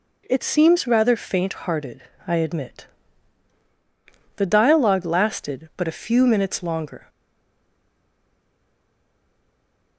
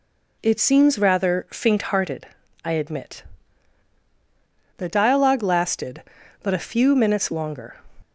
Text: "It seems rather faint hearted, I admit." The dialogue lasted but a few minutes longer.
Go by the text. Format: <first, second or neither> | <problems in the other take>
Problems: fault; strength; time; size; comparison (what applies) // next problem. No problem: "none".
second | stays silent after the last word; strong; from 7.0 s on; 2.9 s long